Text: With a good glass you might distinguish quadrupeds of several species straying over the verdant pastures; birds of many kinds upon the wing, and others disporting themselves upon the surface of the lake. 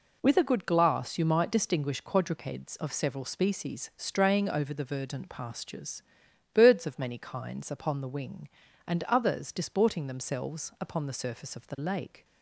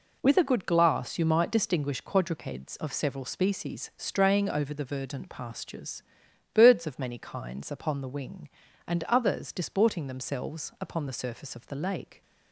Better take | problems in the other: neither | none

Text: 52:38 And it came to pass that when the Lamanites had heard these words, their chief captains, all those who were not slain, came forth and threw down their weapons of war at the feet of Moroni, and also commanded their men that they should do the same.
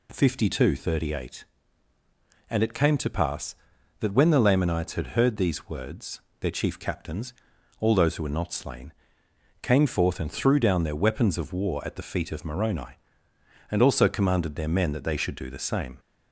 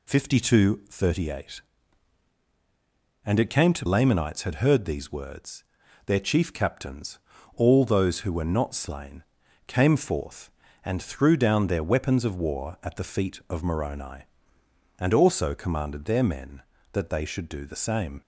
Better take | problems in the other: first | skips "pass that when the"; at 3.8 s

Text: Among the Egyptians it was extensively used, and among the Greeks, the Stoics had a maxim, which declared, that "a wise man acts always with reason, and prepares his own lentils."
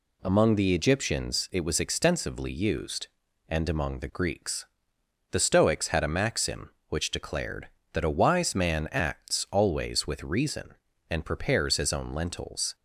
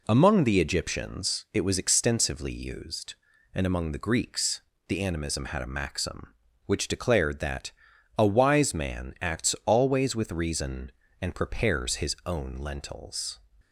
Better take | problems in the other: first | says "Animism" for "Stoics"; at 5.0 s // pauses between "that" and "a"; noticeable; at 7.7 s; 0.47 s long

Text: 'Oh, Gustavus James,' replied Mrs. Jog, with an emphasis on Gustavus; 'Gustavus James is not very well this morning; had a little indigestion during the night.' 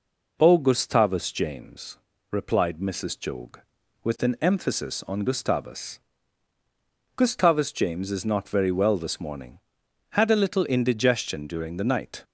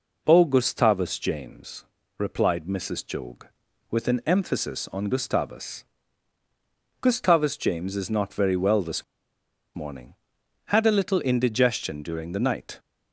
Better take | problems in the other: first | pauses between "this" and "morning"; noticeable; at 9.0 s; 0.70 s long

